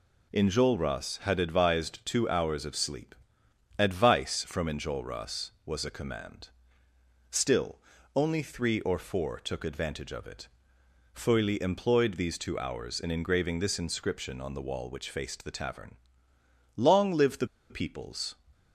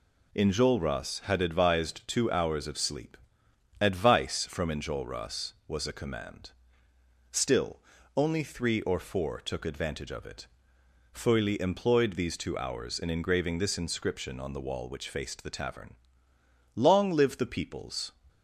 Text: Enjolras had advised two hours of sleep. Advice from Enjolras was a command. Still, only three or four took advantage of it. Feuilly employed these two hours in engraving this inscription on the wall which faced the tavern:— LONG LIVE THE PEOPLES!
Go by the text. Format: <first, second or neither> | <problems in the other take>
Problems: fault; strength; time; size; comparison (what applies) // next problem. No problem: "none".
second | pauses between "THE" and "PEOPLES"; slight; at 17.4 s; 0.23 s long